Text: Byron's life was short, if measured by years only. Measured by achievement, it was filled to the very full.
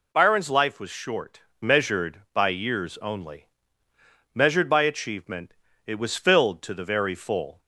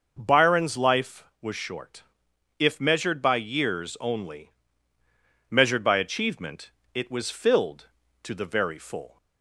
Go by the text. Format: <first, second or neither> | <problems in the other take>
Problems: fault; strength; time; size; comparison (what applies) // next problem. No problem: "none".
second | skips "if"; at 1.5 s